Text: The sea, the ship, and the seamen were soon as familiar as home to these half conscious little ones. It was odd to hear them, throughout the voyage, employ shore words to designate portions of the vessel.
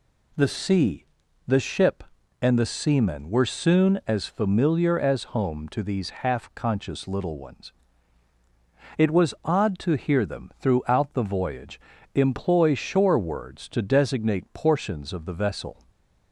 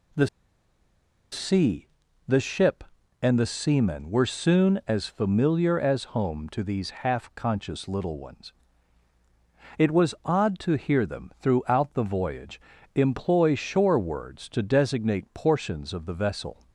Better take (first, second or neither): first